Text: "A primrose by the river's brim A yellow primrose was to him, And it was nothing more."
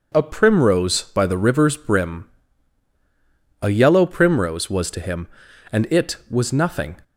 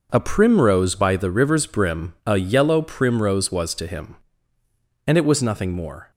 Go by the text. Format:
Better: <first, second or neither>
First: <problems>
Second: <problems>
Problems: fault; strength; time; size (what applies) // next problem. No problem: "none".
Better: second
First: pauses between "brim" and "A"; strong; at 2.2 s; 1.3 s long // stops before "more"; at 7.0 s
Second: none